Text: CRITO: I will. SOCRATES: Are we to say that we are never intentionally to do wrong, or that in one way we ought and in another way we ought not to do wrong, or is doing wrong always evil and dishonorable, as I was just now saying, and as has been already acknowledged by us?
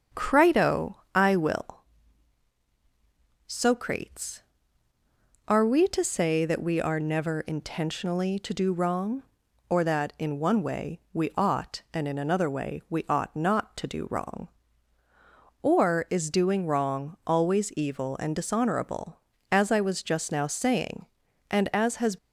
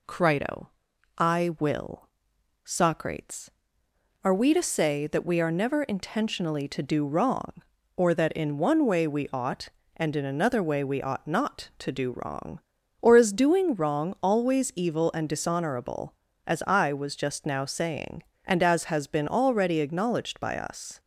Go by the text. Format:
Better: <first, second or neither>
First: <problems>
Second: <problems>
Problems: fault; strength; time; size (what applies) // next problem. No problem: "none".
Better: second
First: starts louder than the rest; strong; until 1.3 s; 7.5 dB // stops before "been already acknowledged by us"; at 22.1 s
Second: none